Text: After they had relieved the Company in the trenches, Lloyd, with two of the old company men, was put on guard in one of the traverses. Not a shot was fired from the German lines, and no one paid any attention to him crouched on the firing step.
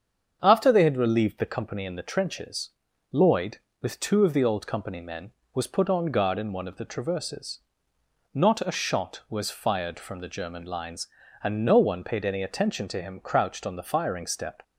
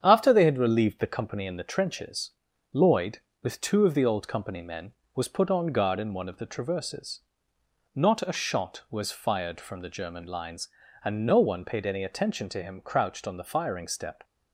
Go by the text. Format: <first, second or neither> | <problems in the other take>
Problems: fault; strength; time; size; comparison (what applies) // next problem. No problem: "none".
first | gets quieter; noticeable; throughout; 4.5 dB // starts louder than the rest; strong; until 1.0 s; 8 dB; strong in the first